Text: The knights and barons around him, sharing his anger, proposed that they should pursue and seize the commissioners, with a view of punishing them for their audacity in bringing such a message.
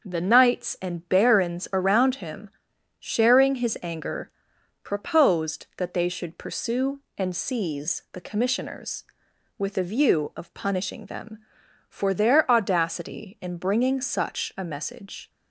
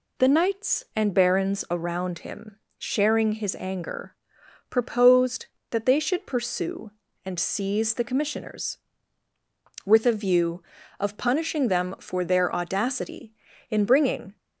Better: first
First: none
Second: stops before "such a message"; at 14.3 s

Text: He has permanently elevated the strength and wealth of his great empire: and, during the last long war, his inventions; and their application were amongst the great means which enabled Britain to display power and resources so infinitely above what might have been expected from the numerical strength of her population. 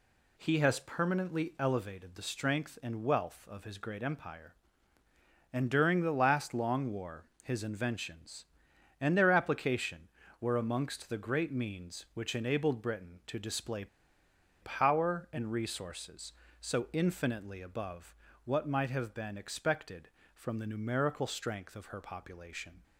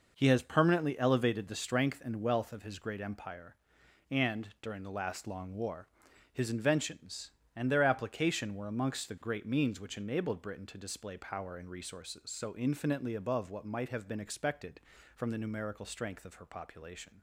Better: second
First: pauses between "display" and "power"; noticeable; at 13.8 s; 0.77 s long // pauses between "above" and "what"; slight; at 18.1 s; 0.30 s long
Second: none

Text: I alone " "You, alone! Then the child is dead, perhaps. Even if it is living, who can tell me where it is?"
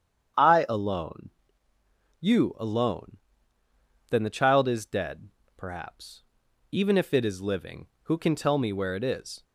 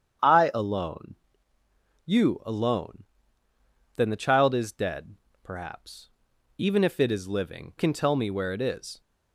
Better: first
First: starts louder than the rest; strong; until 1.8 s; 8.5 dB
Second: starts louder than the rest; strong; until 1.7 s; 8.5 dB // skips "who"; at 7.7 s

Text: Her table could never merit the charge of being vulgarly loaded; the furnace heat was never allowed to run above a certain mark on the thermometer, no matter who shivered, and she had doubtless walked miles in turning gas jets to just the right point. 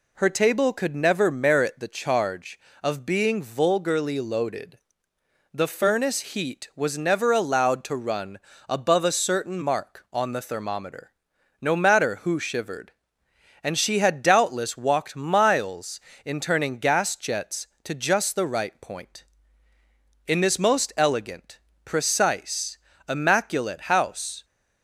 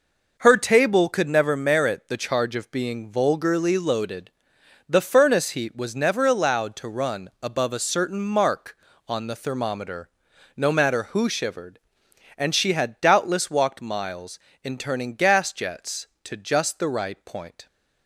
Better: second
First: pauses between "run" and "above"; slight; at 8.3 s; 0.28 s long // goes on to say "In this most elegant precise immaculate house"; strong; from 20.2 s on; 4.1 s long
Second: none

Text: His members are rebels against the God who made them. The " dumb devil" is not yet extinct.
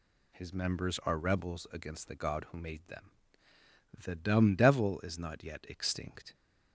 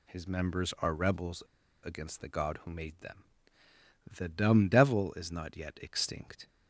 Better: first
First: none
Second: pauses between "rebels" and "against"; at 1.4 s; 0.42 s long

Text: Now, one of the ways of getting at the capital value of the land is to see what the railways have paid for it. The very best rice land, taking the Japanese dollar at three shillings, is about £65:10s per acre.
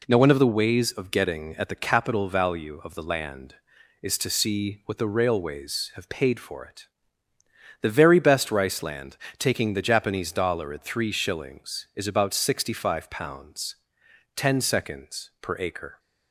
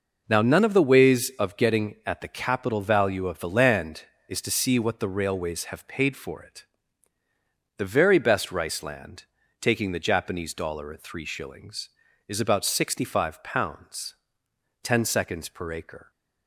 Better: first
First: none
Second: says "none" for "one"; at 0.4 s

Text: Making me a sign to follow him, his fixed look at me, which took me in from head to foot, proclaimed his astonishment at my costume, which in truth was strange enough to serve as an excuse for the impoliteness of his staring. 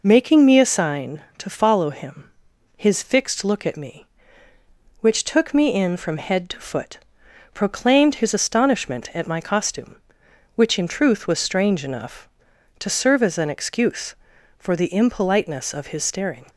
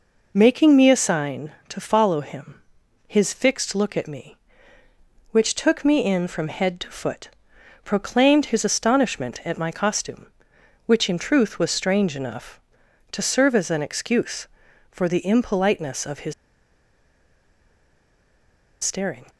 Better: first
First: none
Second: pauses between "his" and "staring"; strong; at 16.3 s; 2.5 s long

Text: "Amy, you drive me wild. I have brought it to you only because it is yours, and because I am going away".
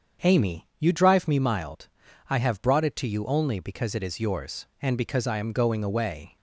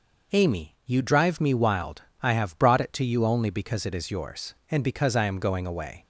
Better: second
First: starts louder than the rest; strong; until 1.3 s; 7 dB // says "mild" for "wild"; at 1.3 s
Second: none

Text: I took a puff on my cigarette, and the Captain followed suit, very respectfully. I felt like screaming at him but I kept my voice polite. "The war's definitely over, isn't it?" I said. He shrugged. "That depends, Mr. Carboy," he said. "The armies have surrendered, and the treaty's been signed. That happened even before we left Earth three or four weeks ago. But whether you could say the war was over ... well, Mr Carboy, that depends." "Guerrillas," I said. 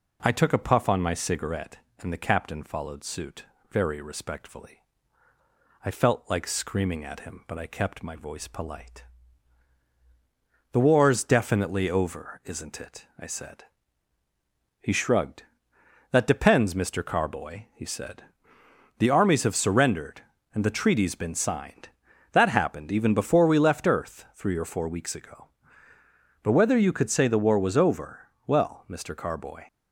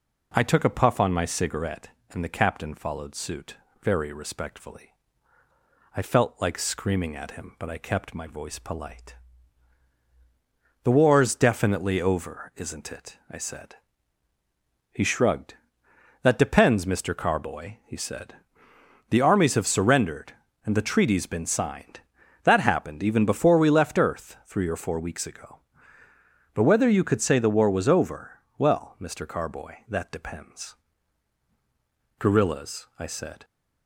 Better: second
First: stops before "that depends Guerrillas I said"; at 29.6 s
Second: none

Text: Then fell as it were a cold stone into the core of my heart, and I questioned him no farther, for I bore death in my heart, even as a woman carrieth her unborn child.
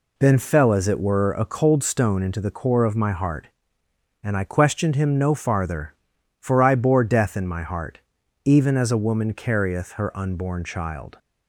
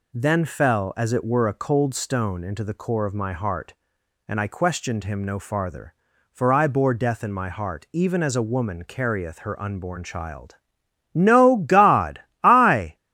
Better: first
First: none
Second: goes on to say "No God I"; strong; from 11.1 s on; 1.8 s long

